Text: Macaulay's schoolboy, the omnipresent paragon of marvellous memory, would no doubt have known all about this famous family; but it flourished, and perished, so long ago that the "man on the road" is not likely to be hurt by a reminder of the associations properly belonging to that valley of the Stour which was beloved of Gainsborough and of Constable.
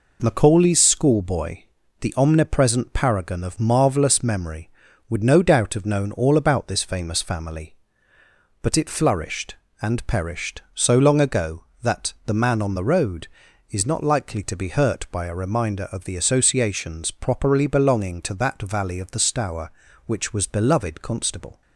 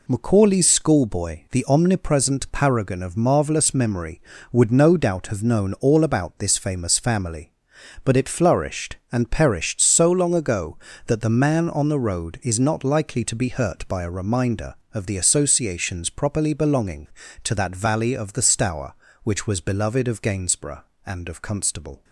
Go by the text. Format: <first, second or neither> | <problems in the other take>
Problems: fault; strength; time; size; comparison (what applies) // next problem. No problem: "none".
second | skips "of Gainsborough and of"; at 21.0 s